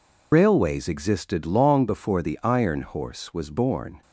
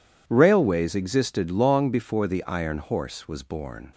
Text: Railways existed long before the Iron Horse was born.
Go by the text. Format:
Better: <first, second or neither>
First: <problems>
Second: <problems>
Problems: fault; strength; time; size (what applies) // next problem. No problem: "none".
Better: second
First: loses the start of "Railways"; at 0.3 s; 110 ms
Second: none